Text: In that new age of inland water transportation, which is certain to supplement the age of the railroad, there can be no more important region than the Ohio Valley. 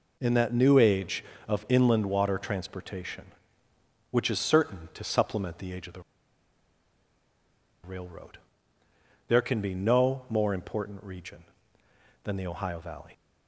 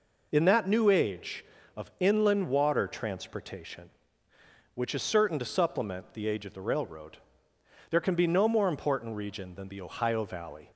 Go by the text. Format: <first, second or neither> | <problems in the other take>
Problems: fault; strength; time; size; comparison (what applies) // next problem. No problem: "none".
second | pauses between "the" and "railroad"; strong; at 5.9 s; 1.8 s long